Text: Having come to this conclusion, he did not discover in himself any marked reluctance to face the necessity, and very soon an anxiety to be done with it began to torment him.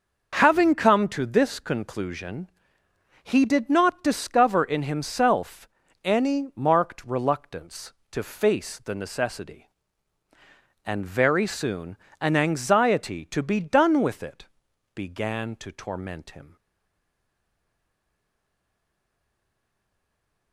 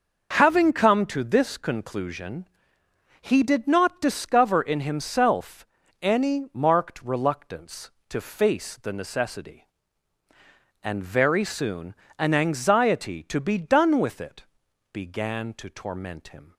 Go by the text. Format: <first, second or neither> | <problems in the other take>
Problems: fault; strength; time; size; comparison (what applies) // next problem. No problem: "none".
second | starts louder than the rest; noticeable; until 1.4 s; 6 dB; noticeable in the second // pauses between "himself" and "any"; slight; at 5.6 s; 0.36 s long; slight in the second // pauses between "soon" and "an"; slight; at 11.9 s; 0.24 s long; slight in the second // pauses between "it" and "began"; noticeable; at 14.4 s; 0.50 s long; noticeable in the second // stays silent after the last word; strong; from 16.5 s on; 4.0 s long